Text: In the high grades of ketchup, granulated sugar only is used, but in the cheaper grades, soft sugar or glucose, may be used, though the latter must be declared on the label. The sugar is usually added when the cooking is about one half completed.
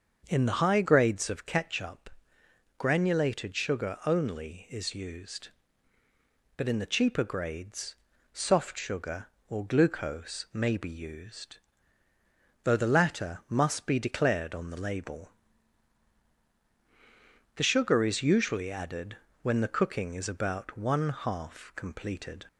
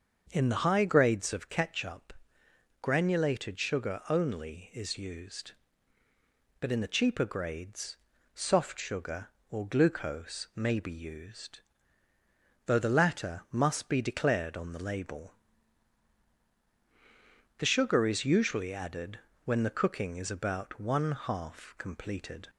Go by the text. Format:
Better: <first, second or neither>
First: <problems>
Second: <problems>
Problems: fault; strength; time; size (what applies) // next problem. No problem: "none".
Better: neither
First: starts louder than the rest; until 1.2 s; 6.5 dB // pauses between "added" and "when"; slight; at 19.1 s; 0.24 s long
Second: starts louder than the rest; until 1.3 s; 6.5 dB // pauses between "added" and "when"; slight; at 19.1 s; 0.24 s long